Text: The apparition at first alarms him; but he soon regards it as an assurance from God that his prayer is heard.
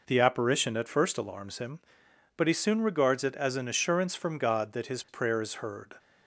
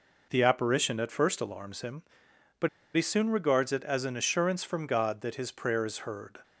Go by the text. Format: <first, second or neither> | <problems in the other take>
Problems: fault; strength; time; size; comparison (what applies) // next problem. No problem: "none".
first | pauses between "but" and "he"; slight; at 2.6 s; 0.26 s long